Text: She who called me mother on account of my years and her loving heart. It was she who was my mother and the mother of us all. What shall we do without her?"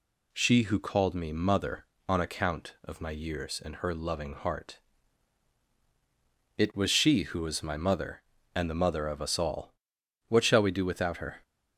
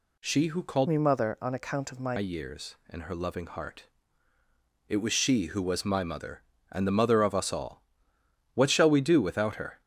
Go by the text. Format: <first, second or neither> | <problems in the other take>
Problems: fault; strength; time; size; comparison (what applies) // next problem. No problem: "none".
first | changes voice from "me" to "my"; from 0.8 to 2.1 s; 1.3 s long